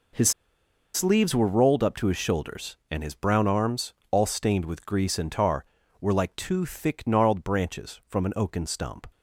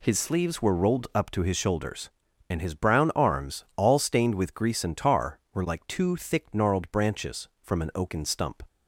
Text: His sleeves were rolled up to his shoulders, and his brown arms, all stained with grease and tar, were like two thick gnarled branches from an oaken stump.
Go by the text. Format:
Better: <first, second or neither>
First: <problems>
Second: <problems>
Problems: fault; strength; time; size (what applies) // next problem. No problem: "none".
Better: second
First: pauses between "His" and "sleeves"; noticeable; at 0.3 s; 0.64 s long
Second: none